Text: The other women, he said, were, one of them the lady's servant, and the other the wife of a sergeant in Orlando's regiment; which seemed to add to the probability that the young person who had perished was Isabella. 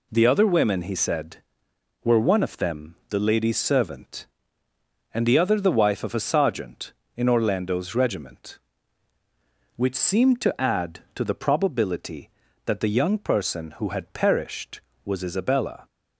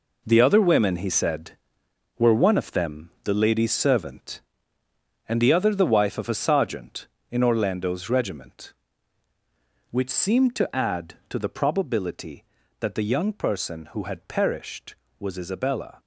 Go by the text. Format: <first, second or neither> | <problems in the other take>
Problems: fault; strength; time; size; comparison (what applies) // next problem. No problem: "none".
first | gets quieter; strong; throughout; 9.5 dB